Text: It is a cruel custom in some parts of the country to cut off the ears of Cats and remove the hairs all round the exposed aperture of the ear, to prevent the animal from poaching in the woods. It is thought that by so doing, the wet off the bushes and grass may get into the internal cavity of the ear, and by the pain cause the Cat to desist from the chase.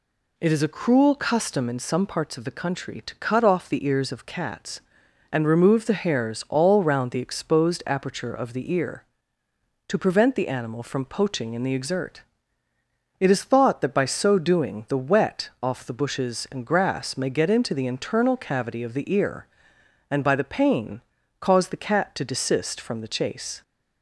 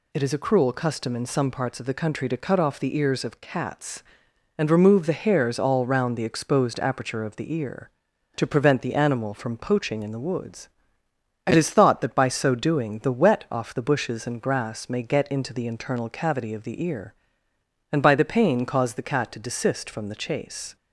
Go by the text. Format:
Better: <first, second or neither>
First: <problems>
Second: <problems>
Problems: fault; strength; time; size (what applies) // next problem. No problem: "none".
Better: second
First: says "exert" for "woods"; at 11.7 s // pauses between "pain" and "cause"; at 21.0 s; 0.40 s long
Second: none